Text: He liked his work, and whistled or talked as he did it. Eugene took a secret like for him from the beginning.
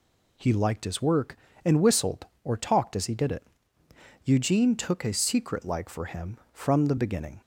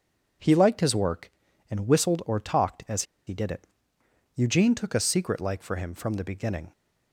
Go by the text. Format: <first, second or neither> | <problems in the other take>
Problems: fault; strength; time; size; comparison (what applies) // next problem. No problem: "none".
first | pauses between "as" and "he"; slight; at 3.0 s; 0.24 s long